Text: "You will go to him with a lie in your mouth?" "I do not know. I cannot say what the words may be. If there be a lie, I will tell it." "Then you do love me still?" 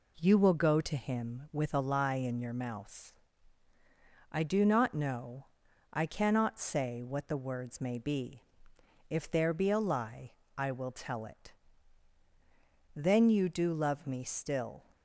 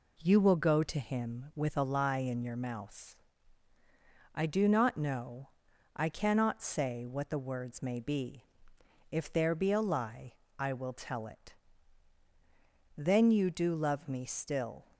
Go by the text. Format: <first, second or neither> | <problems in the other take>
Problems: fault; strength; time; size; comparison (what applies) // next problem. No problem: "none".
neither | none